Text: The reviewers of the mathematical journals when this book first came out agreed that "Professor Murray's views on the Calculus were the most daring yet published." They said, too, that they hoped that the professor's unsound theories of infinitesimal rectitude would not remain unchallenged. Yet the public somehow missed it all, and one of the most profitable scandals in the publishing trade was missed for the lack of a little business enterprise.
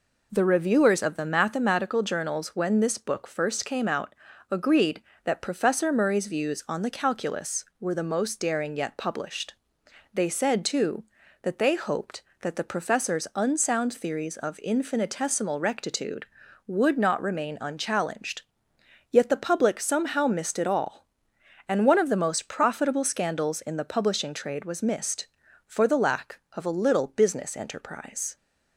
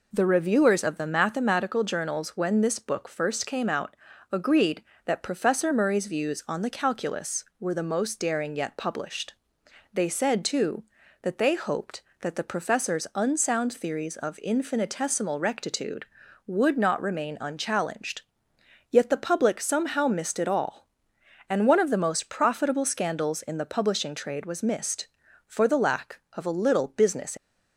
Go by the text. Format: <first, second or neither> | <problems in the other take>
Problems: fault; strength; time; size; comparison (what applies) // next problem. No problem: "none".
first | pauses between "out" and "agreed"; slight; at 3.9 s; 0.34 s long; slight in the first // stops before "enterprise"; at 27.3 s